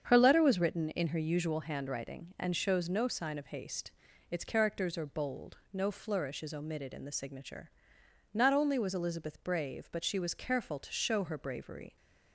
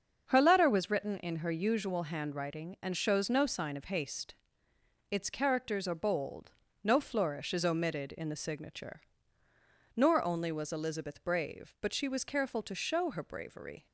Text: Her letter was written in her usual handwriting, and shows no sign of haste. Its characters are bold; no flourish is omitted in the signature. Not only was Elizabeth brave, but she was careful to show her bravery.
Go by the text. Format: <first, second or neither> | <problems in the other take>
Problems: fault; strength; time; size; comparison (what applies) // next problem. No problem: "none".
first | starts louder than the rest; until 1.3 s; 6.5 dB; strong in the first // says "Nor" for "Not"; at 9.9 s